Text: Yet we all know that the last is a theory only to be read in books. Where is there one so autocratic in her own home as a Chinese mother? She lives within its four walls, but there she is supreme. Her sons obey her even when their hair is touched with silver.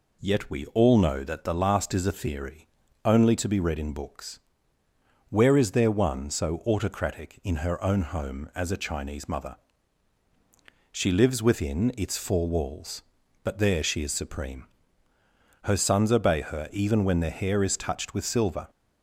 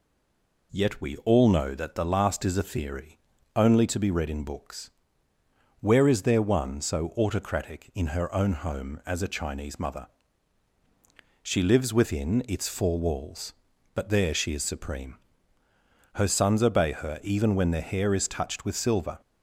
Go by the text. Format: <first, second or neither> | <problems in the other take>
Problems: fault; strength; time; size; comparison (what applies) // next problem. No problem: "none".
first | stays silent before the first word; slight; until 0.7 s; 0.7 s long // pauses between "theory" and "only"; at 3.1 s; 0.38 s long; also in the first